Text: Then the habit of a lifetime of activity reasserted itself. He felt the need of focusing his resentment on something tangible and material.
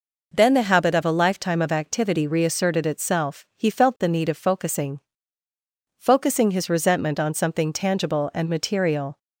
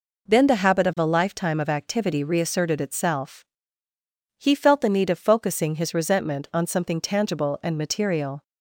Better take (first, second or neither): second